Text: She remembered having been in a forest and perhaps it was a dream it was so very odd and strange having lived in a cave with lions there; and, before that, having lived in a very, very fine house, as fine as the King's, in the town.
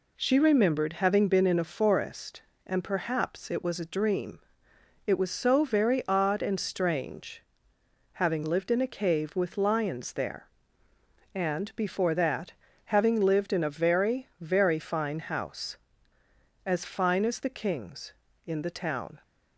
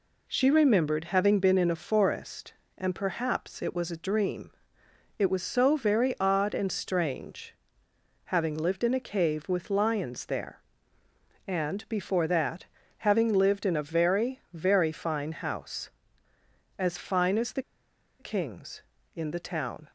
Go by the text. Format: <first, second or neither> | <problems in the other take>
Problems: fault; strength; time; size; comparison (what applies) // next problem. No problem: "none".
first | pauses between "dream" and "it"; noticeable; at 4.5 s; 0.68 s long; noticeable in the first // pauses between "strange" and "having"; noticeable; at 7.5 s; 0.70 s long; noticeable in the first // pauses between "the" and "King's"; noticeable; at 17.6 s; 0.56 s long